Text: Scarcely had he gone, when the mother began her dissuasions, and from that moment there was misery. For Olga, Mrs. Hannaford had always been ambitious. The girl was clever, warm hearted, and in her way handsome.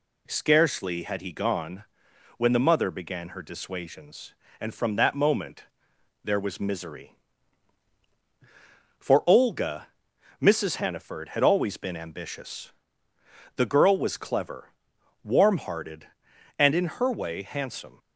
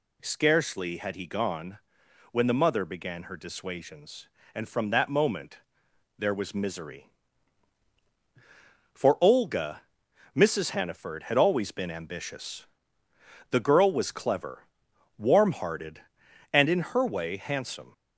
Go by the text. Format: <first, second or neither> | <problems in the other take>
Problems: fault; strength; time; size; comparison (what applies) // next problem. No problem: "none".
first | gets louder; slight; throughout; 2.5 dB // pauses between "moment" and "there"; noticeable; at 5.5 s; 0.60 s long; noticeable in the first